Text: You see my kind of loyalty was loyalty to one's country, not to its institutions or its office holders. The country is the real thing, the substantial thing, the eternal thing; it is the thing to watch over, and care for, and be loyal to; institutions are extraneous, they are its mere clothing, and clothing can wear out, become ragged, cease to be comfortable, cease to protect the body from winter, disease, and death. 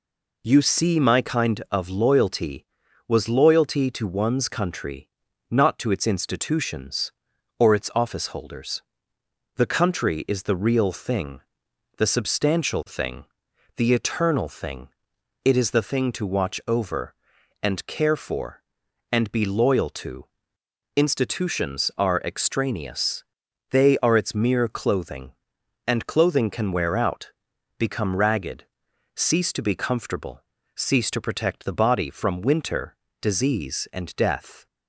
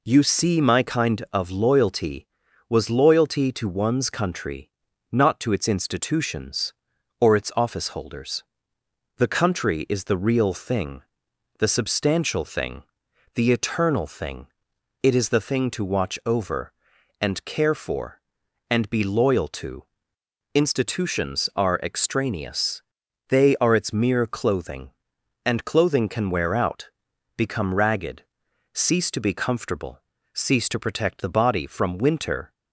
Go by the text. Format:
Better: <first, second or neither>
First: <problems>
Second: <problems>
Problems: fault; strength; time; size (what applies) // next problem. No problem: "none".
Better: first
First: none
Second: stops before "disease and death"; at 32.5 s